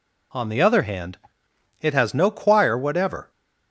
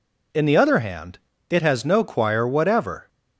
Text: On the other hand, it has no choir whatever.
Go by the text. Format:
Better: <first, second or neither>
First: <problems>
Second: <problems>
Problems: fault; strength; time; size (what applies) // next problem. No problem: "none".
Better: first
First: none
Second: says "In" for "On"; at 0.3 s